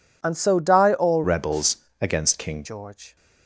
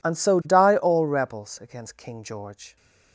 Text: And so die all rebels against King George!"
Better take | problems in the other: second | changes voice from "rebels" to "King"; from 1.2 to 2.6 s; 1.4 s long // pauses between "rebels" and "against"; slight; at 1.7 s; 0.24 s long

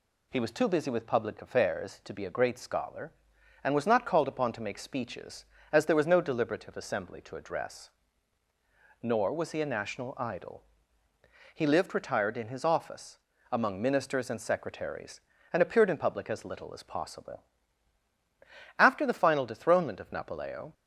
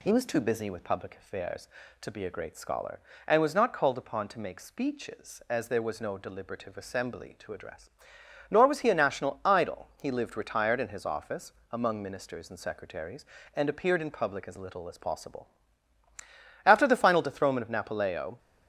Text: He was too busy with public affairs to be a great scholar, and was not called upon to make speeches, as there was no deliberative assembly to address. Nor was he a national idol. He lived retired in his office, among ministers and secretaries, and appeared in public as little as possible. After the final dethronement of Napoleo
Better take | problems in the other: neither | none

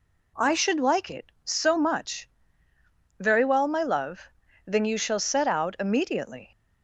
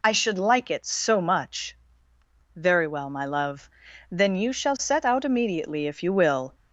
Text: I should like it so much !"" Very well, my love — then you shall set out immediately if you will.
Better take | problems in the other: second | stops before "if you will"; at 6.5 s

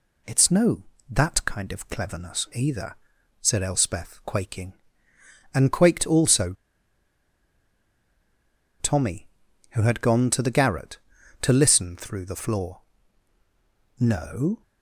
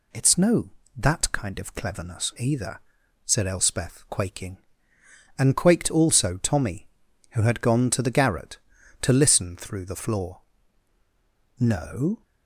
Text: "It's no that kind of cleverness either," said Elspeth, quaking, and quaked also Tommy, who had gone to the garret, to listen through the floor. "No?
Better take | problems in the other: second | pauses between "also" and "Tommy"; strong; at 6.5 s; 2.2 s long

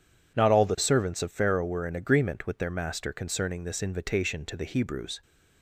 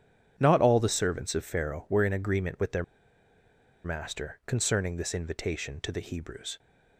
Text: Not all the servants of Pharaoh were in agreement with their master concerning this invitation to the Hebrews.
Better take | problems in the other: first | starts louder than the rest; strong; until 1.3 s; 9 dB // pauses between "their" and "master"; at 2.8 s; 1.0 s long

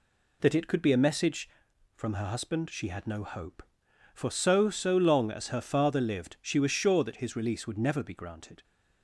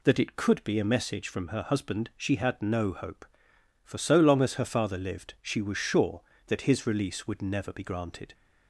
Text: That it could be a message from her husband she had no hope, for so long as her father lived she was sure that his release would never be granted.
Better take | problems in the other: second | says "so" twice; at 4.7 s

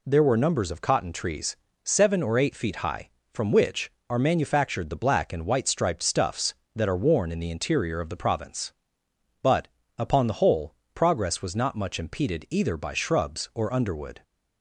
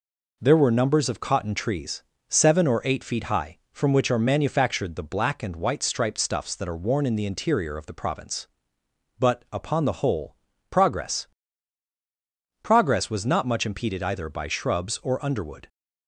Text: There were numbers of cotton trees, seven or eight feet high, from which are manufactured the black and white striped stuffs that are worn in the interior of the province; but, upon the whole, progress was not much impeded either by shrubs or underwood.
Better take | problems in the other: first | says "progress" twice; at 12.6 s

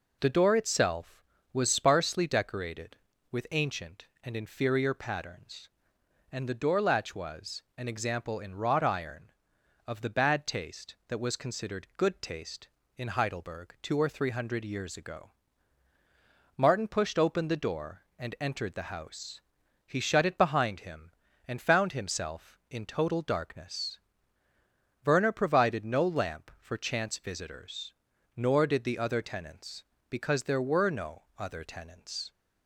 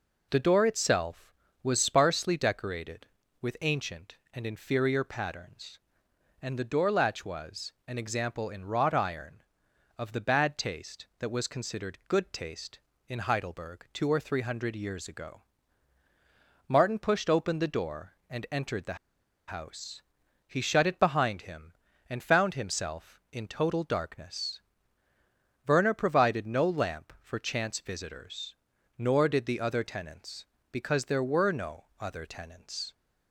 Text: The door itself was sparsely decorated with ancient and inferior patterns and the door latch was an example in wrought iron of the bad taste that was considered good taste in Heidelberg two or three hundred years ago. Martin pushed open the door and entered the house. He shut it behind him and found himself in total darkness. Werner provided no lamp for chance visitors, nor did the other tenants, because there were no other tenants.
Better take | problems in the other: first | pauses between "the" and "house"; noticeable; at 18.9 s; 0.52 s long

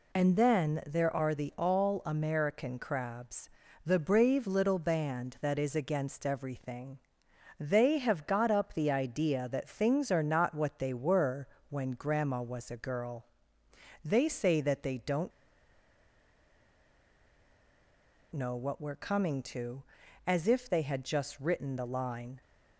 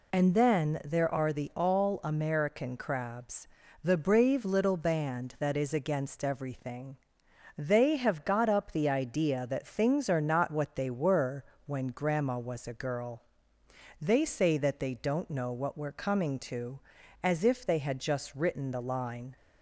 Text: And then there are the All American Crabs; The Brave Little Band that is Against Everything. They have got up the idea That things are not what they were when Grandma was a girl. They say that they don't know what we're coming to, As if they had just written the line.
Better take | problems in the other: second | pauses between "were" and "when"; slight; at 11.4 s; 0.22 s long; slight in the second // pauses between "don't" and "know"; strong; at 15.3 s; 3.0 s long

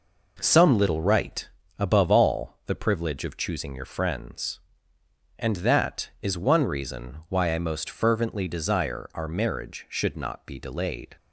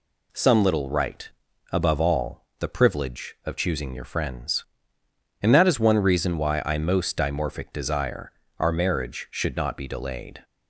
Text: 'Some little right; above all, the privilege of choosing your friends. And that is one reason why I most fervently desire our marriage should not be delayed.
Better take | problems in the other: first | says "dimorphic" for "fervently"; at 7.1 s // pauses between "desire" and "our"; slight; at 8.3 s; 0.28 s long

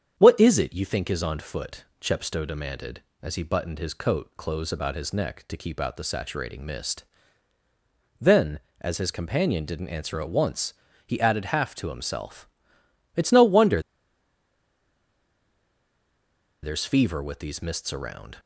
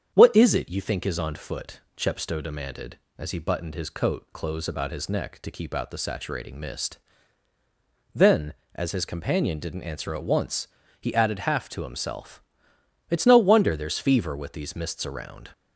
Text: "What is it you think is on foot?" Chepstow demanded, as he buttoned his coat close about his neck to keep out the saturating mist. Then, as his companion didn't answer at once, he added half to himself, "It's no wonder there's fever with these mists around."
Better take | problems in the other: second | starts louder than the rest; strong; until 1.1 s; 8 dB; strong in the second // pauses between "wonder" and "there's"; strong; at 13.7 s; 2.8 s long

